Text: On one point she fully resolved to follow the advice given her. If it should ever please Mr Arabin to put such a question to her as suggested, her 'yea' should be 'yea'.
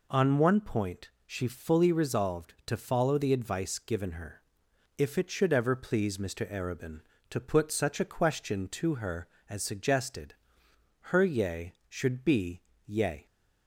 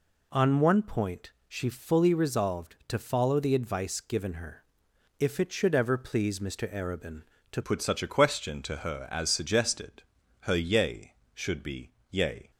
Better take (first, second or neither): first